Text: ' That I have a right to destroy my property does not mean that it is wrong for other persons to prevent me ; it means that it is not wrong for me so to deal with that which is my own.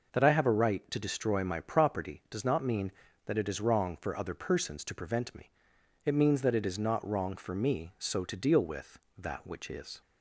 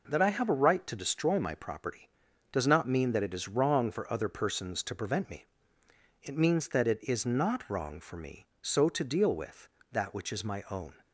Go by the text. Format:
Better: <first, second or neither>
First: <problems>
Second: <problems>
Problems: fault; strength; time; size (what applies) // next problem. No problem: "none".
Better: second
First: stops before "my own"; at 10.0 s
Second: none